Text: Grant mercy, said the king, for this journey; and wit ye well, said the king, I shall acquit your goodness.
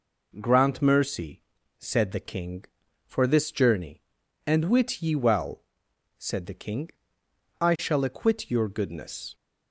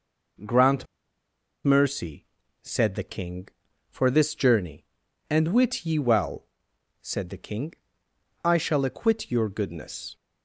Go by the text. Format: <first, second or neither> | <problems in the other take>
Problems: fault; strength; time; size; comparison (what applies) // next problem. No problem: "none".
first | pauses between "Grant" and "mercy"; noticeable; at 0.8 s; 0.79 s long